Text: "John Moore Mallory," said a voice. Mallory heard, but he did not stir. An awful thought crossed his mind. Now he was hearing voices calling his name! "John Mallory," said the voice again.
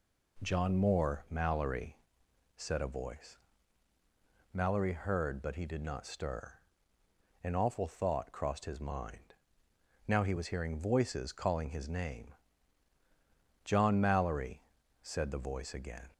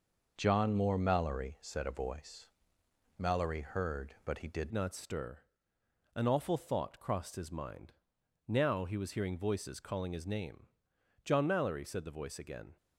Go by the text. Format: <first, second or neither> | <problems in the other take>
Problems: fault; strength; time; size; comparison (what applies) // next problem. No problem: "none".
first | changes voice at "not"; from 4.7 s on; 8.0 s long